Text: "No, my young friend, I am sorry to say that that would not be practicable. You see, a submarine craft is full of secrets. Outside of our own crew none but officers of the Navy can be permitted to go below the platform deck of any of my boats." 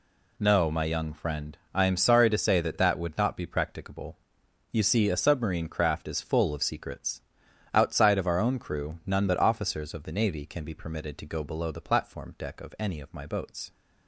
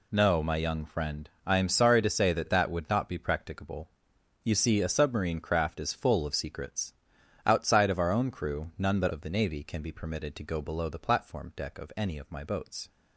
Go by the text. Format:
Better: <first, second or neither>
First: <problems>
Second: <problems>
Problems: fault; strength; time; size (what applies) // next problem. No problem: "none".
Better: first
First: none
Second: skips "officers"; at 9.1 s